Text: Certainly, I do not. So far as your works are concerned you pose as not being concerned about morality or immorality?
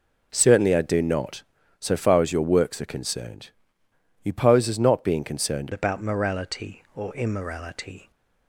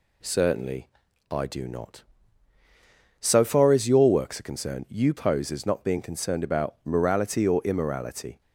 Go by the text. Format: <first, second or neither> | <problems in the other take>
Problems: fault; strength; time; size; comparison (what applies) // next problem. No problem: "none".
second | pauses between "concerned" and "you"; noticeable; at 3.4 s; 0.72 s long // changes voice at "about"; from 5.7 s on; 2.4 s long